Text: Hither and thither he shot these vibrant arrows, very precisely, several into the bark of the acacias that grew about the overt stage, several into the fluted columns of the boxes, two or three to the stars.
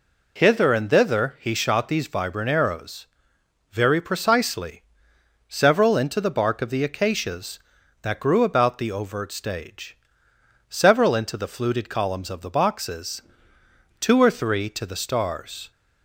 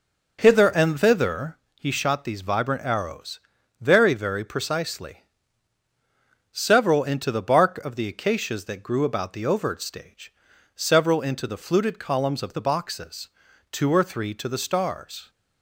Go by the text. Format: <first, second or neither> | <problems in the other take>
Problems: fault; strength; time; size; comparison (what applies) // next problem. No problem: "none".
first | pauses between "thither" and "he"; slight; at 1.5 s; 0.20 s long // says "very" twice; at 4.1 s